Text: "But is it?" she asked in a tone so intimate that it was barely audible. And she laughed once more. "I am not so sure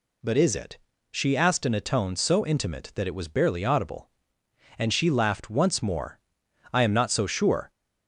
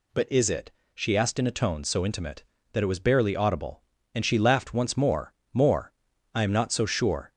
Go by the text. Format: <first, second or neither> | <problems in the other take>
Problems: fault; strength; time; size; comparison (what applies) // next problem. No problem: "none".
first | says "more" twice; at 5.5 s